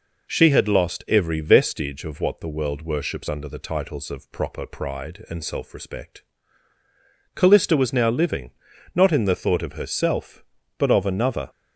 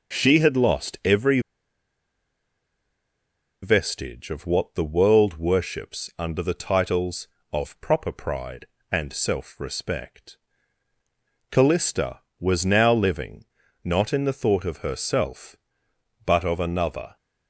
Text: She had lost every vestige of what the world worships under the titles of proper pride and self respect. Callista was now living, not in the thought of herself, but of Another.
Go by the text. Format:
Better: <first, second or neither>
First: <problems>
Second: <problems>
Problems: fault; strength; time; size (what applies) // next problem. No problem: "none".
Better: first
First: none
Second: pauses between "every" and "vestige"; strong; at 1.3 s; 2.2 s long